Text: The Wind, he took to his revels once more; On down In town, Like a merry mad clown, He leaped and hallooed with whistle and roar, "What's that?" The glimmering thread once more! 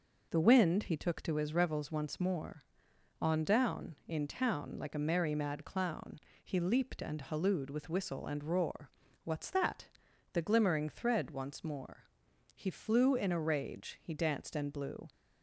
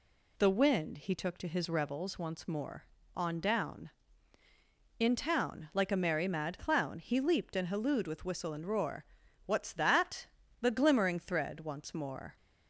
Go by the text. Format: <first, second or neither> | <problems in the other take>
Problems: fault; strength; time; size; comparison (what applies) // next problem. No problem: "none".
second | goes on to say "He flew in a rage he danced and blew"; strong; from 12.5 s on; 2.5 s long